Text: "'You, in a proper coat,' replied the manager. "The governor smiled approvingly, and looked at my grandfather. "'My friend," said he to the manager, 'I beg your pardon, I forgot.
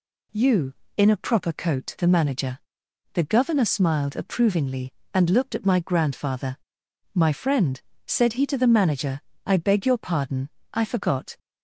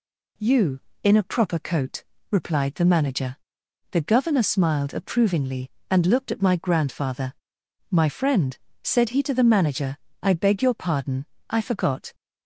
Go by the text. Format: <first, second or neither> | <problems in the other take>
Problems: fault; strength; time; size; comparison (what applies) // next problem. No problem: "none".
second | skips "replied"; at 1.9 s